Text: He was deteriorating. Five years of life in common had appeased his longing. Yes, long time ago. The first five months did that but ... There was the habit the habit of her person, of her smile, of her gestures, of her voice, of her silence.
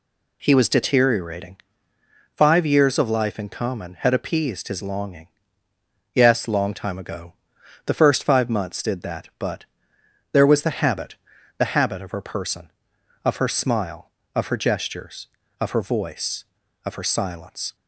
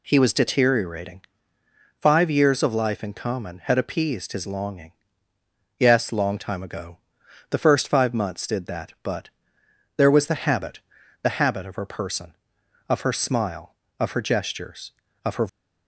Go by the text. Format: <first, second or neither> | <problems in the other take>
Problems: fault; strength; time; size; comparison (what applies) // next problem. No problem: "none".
first | pauses between "habit" and "the"; at 10.7 s; 0.44 s long; also in the first // stops before "voice of her silence"; at 15.4 s